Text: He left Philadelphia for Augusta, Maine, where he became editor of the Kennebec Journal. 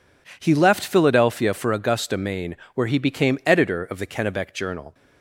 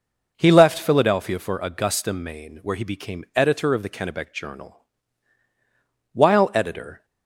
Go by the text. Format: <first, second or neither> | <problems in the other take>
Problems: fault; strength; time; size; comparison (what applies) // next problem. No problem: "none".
first | goes on to say "While editor"; noticeable; from 6.1 s on; 0.92 s long